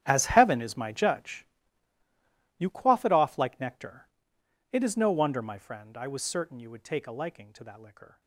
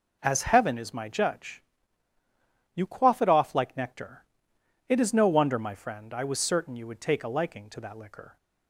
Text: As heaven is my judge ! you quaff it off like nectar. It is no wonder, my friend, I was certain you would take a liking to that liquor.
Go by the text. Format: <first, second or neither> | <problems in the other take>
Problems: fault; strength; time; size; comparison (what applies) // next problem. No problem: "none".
second | gets quieter; strong; throughout; 17 dB